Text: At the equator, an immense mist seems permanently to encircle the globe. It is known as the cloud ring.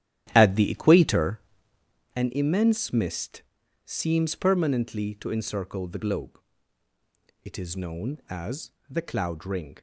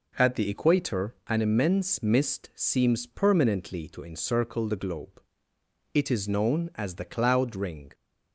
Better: second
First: starts louder than the rest; strong; until 2.1 s; 12.5 dB // pauses between "mist" and "seems"; at 3.4 s; 0.44 s long // pauses between "as" and "the"; slight; at 8.6 s; 0.20 s long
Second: none

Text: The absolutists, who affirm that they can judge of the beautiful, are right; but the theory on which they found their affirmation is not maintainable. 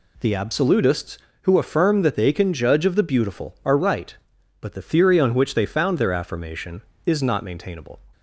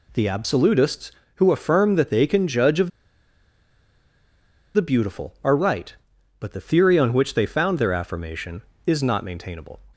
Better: first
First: none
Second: pauses between "of" and "the"; strong; at 2.8 s; 1.8 s long

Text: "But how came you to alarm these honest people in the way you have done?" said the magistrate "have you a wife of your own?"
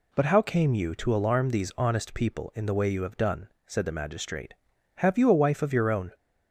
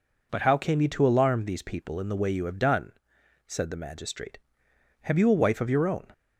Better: first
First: none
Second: skips "honest"; at 1.6 s

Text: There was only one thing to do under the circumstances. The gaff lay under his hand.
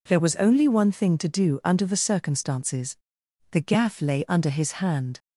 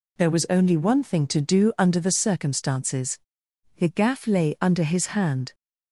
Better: neither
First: none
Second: none

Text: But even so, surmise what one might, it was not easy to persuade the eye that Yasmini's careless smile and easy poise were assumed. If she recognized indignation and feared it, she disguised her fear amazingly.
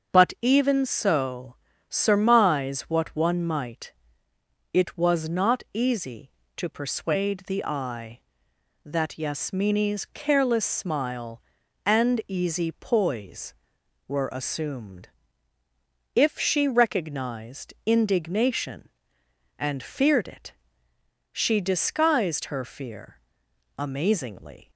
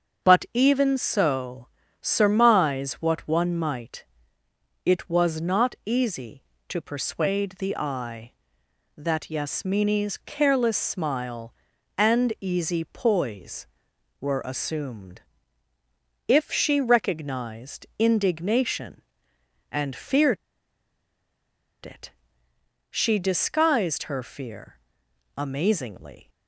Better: first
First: starts louder than the rest; until 1.2 s; 6.5 dB // pauses between "fear" and "amazingly"; noticeable; at 23.1 s; 0.60 s long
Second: starts louder than the rest; until 1.3 s; 6.5 dB // pauses between "feared" and "it"; strong; at 20.3 s; 1.4 s long // pauses between "fear" and "amazingly"; noticeable; at 24.7 s; 0.60 s long

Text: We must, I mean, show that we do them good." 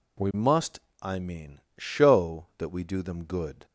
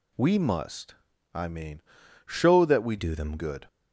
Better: first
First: none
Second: changes voice from "do" to "them"; from 2.9 to 3.3 s; 0.4 s long

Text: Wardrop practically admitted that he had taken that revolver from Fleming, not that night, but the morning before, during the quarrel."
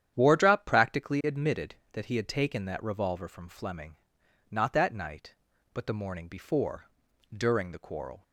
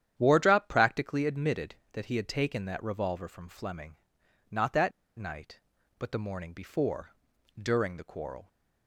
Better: first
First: starts louder than the rest; strong; until 1.1 s; 9.5 dB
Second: starts louder than the rest; strong; until 1.1 s; 9.5 dB // pauses between "that" and "night"; slight; at 4.9 s; 0.26 s long

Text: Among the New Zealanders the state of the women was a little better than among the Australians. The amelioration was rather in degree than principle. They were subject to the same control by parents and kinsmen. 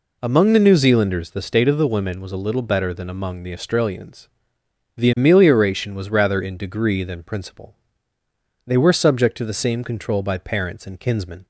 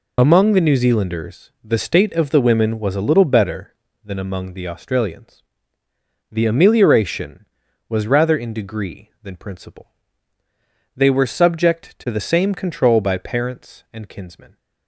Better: first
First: none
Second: loses the start of "Among"; at 0.1 s; 40 ms

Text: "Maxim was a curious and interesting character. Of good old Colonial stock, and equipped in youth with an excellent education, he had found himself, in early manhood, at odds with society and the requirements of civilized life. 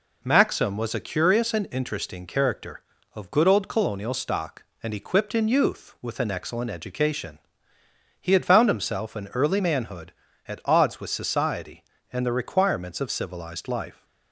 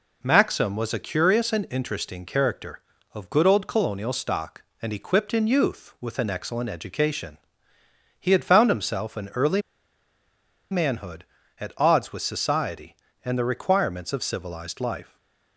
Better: first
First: none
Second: pauses between "early" and "manhood"; at 9.6 s; 1.1 s long // stays silent after the last word; slight; from 15.0 s on; 0.5 s long

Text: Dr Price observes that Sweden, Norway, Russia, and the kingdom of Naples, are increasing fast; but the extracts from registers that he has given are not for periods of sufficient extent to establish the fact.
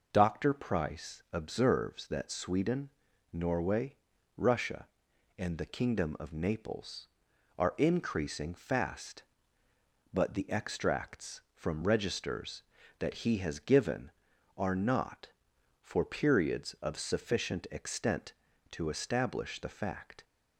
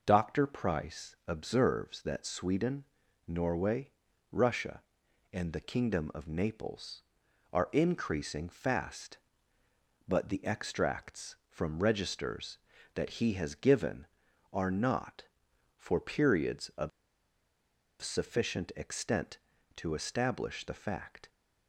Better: first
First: none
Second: pauses between "of" and "sufficient"; at 16.9 s; 1.1 s long

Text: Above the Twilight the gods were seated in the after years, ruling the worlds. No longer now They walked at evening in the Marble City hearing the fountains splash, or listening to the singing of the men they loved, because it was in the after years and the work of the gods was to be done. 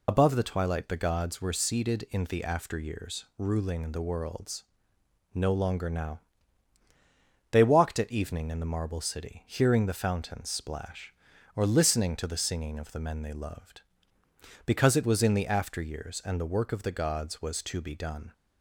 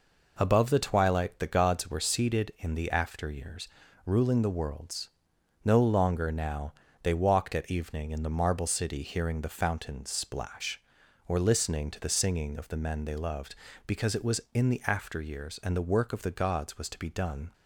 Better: second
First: loses the start of "Above"; at 0.0 s; 50 ms // pauses between "now" and "They"; strong; at 6.2 s; 1.3 s long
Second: pauses between "now" and "They"; slight; at 6.7 s; 0.28 s long

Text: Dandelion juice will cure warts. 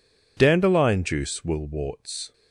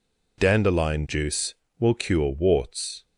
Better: second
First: skips "cure"; at 1.6 s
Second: none

